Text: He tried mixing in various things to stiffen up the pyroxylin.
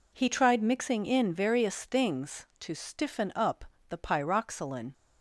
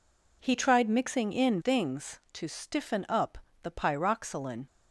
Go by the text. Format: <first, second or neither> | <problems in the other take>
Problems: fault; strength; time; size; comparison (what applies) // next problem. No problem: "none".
first | skips "various"; at 1.5 s // pauses between "up" and "the"; slight; at 3.3 s; 0.24 s long; slight in the first